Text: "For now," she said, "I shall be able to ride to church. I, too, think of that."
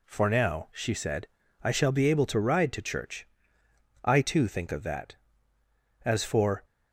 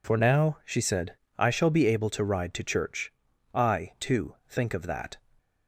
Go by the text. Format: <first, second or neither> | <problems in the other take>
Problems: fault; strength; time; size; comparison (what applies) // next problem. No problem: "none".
second | goes on to say "As for"; from 6.0 s on; 0.60 s long